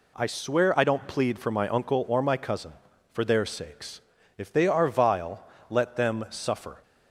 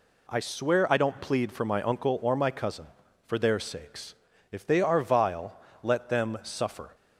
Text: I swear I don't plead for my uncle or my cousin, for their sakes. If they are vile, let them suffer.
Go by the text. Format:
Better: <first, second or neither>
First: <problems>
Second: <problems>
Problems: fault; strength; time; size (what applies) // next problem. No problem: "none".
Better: neither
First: none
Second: none